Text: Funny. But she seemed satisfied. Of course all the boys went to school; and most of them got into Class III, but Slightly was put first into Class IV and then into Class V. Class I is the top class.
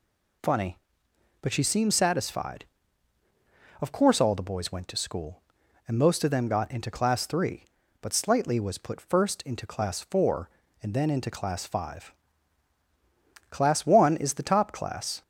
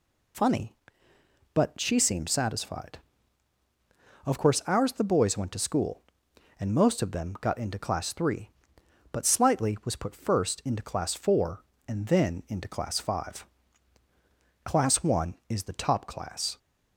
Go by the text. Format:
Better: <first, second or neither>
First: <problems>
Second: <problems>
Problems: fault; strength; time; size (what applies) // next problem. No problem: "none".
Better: first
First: none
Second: says "ours" for "all"; at 4.6 s